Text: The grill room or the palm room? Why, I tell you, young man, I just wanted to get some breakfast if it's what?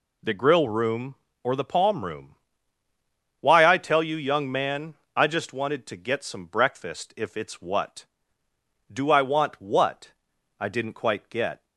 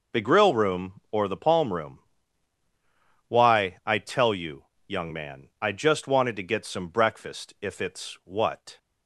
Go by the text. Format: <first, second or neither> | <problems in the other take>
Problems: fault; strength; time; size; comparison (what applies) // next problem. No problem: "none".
second | goes on to say "Do I want what I didn't quite get"; strong; from 8.9 s on; 2.7 s long